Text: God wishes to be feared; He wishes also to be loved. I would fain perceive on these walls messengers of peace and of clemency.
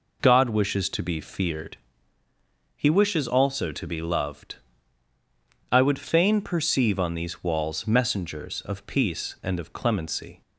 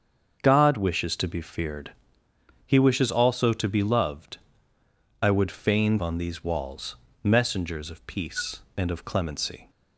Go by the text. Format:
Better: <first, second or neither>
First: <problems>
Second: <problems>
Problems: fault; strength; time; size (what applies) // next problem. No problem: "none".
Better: first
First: none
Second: starts louder than the rest; until 1.4 s; 6.5 dB // skips "perceive"; at 5.9 s // pauses between "walls" and "messengers"; slight; at 6.9 s; 0.30 s long